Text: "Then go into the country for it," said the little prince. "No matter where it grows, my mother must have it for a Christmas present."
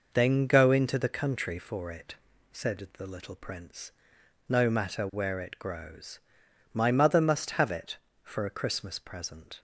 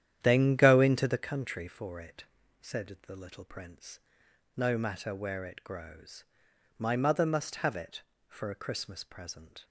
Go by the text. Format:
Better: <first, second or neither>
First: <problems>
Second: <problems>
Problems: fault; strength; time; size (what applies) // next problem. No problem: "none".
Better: first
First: none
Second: starts louder than the rest; strong; until 1.3 s; 10.5 dB